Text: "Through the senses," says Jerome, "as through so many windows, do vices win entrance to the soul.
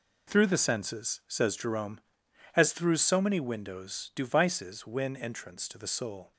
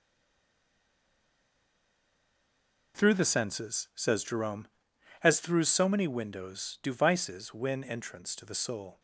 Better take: first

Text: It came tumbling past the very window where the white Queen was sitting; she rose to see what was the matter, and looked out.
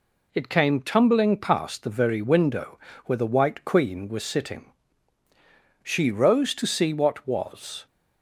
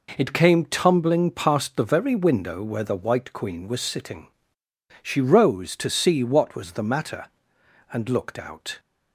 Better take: second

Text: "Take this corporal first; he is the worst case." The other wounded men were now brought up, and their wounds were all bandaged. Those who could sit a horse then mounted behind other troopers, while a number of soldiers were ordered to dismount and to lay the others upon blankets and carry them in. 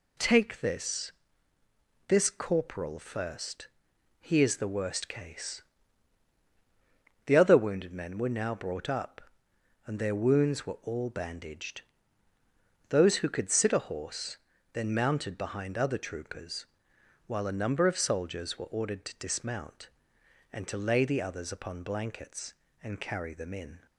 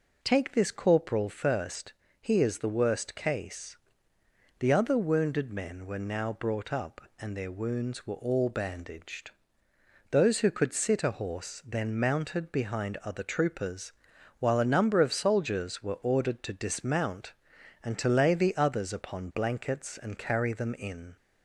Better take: second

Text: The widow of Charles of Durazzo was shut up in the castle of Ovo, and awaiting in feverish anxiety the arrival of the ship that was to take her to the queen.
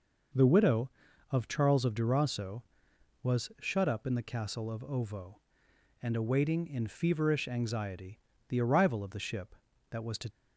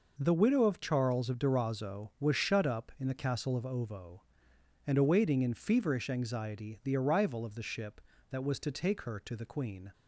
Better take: second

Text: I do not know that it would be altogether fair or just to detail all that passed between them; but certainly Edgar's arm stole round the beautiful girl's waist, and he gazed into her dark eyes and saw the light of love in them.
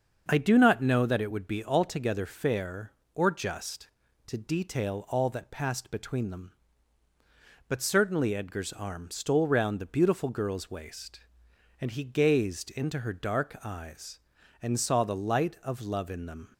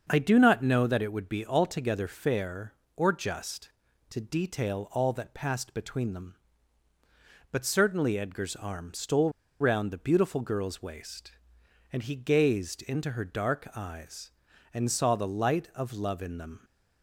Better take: first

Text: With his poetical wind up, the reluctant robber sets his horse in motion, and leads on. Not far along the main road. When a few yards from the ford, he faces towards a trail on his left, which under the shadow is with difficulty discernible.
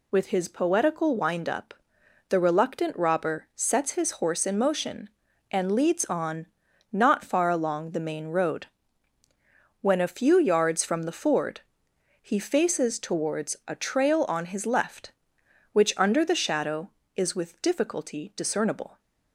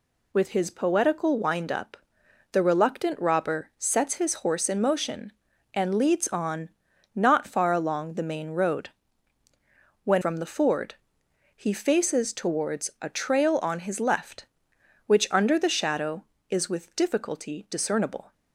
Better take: first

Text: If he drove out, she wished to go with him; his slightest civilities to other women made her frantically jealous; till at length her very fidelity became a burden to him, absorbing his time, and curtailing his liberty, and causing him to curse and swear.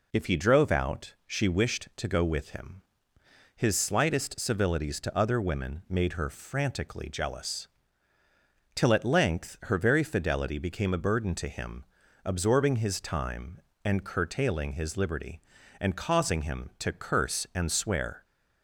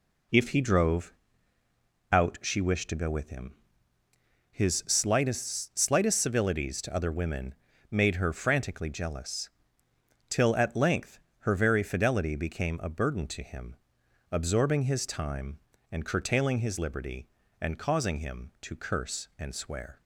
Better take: first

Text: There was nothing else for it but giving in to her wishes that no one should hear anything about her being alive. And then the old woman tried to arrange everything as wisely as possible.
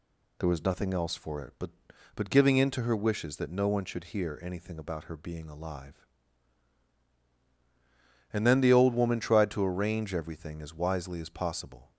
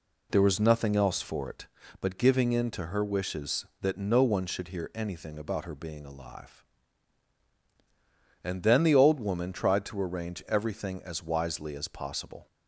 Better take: second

